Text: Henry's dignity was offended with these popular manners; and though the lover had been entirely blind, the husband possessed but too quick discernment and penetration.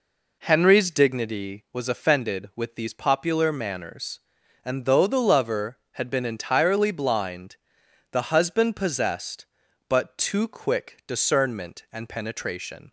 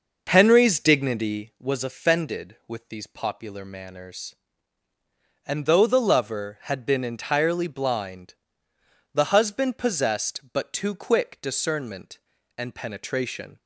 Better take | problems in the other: first | starts louder than the rest; noticeable; until 1.5 s; 6 dB

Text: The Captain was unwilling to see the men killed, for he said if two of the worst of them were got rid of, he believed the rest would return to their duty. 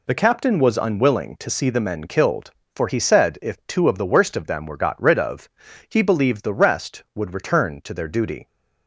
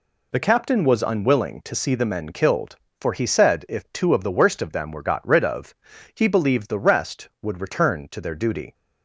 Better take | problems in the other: neither | none

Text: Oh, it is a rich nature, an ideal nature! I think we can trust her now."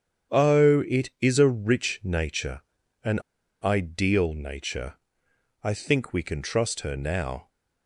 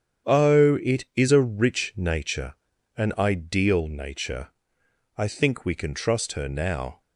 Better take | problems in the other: second | starts louder than the rest; strong; until 1.5 s; 8.5 dB; strong in the second // pauses between "an" and "ideal"; at 3.1 s; 0.45 s long

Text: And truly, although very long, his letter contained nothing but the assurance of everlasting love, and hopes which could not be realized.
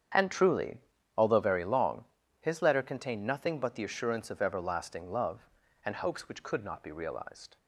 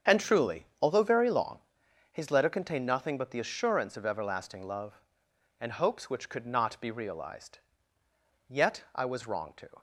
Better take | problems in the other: first | starts louder than the rest; strong; until 1.2 s; 7 dB; strong in the first // goes on to say "Yet I was wrong to"; from 8.4 s on; 1.3 s long

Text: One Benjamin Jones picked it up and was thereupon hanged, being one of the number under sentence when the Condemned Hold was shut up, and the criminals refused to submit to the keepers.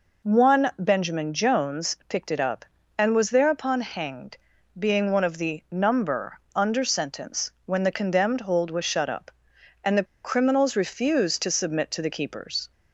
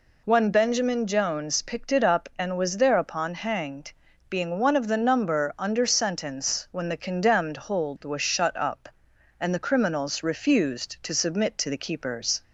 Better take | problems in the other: second | pauses between "number" and "under"; slight; at 6.3 s; 0.16 s long // pauses between "the" and "criminals"; slight; at 10.0 s; 0.20 s long

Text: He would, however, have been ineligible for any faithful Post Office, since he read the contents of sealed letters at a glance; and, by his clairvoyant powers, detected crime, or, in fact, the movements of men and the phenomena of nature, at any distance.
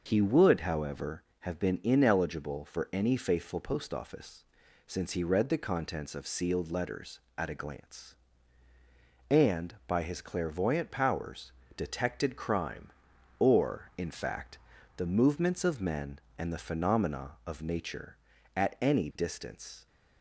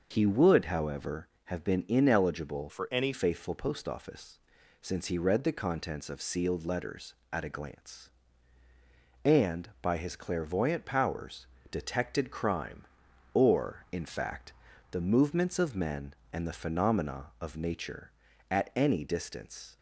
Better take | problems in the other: first | changes voice from "for" to "any"; from 2.6 to 3.1 s; 0.5 s long

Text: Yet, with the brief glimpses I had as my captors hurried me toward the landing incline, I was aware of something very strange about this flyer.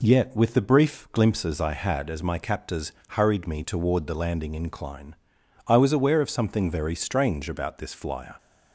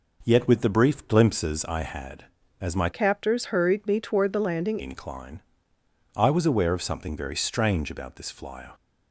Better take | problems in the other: first | changes voice from "captors" to "landing"; from 2.9 to 4.7 s; 1.8 s long

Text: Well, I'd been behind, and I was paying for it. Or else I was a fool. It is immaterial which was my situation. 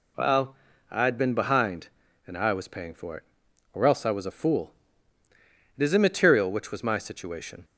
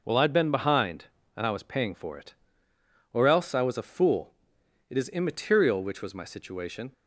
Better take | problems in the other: neither | none

